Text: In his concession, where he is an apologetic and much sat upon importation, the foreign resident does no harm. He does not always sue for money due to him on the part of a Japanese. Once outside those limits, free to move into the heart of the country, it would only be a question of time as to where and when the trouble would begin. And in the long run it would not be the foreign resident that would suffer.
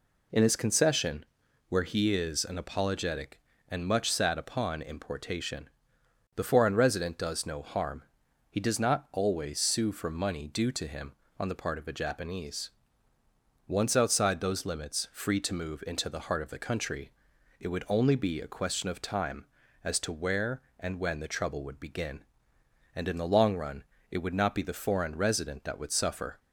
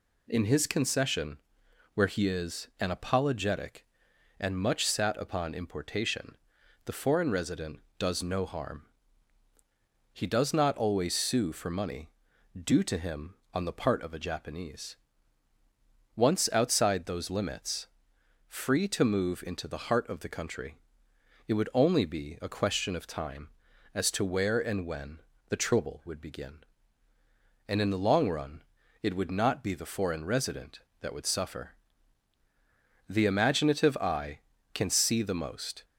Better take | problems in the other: first | pauses between "money" and "due"; noticeable; at 12.0 s; 0.52 s long // pauses between "when" and "the"; slight; at 25.1 s; 0.28 s long // pauses between "run" and "it"; at 28.5 s; 0.40 s long; slight in the first // goes on to say "The imaginative eye can see the most"; strong; from 33.0 s on; 2.7 s long

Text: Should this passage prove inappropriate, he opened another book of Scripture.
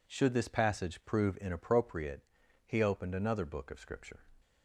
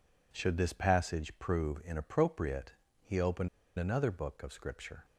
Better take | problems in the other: first | pauses between "opened" and "another"; slight; at 3.4 s; 0.30 s long

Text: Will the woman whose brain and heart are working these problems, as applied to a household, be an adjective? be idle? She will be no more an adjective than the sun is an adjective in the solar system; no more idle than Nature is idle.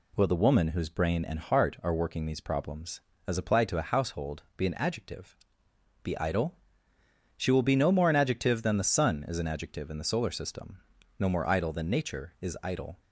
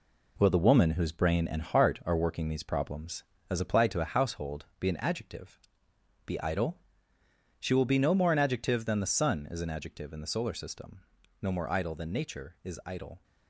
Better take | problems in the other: first | gets quieter; throughout; 7 dB

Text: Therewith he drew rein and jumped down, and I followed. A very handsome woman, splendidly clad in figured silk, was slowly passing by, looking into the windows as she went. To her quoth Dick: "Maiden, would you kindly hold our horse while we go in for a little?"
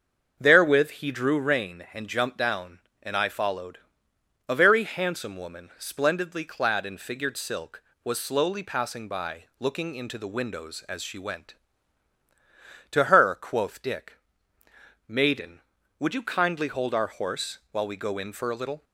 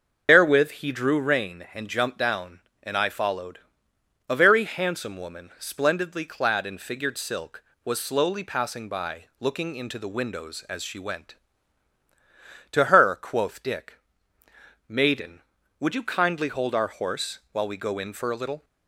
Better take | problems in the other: first | loses the start of "Therewith"; at 0.2 s; 90 ms // starts louder than the rest; until 1.3 s; 6.5 dB; also in the first

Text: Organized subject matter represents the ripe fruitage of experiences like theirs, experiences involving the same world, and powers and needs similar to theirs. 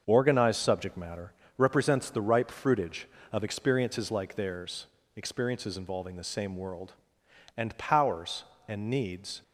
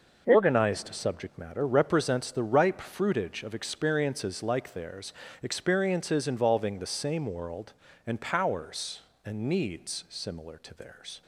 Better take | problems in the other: second | starts louder than the rest; until 1.0 s; 6.5 dB // pauses between "matter" and "represents"; slight; at 1.3 s; 0.24 s long // stops before "similar to theirs"; at 9.4 s

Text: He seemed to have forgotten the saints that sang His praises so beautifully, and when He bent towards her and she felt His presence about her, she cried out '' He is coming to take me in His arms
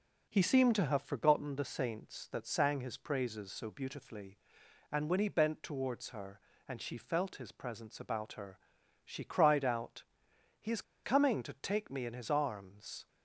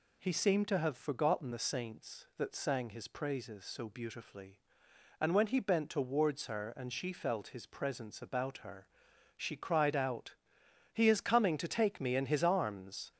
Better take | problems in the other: second | pauses between "is" and "coming"; slight; at 10.8 s; 0.22 s long

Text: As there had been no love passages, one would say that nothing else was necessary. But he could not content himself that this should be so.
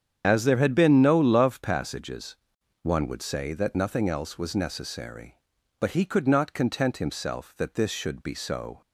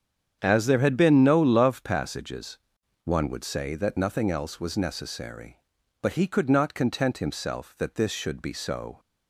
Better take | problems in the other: second | loses the start of "As"; at 0.2 s; 60 ms // starts louder than the rest; strong; until 1.2 s; 8 dB; strong in the second

